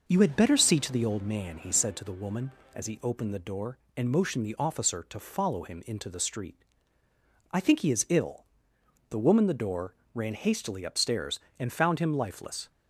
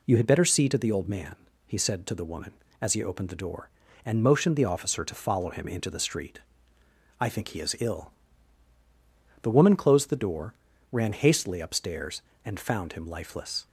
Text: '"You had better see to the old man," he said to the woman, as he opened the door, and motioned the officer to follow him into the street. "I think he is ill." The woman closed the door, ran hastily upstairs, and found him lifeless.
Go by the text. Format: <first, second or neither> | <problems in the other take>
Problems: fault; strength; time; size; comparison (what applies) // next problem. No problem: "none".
second | skips "closed"; at 9.4 s